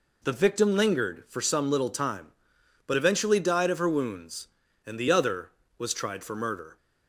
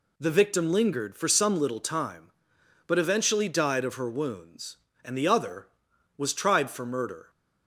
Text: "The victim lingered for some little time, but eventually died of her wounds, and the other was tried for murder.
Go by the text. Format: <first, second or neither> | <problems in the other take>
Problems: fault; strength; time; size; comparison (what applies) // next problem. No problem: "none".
neither | none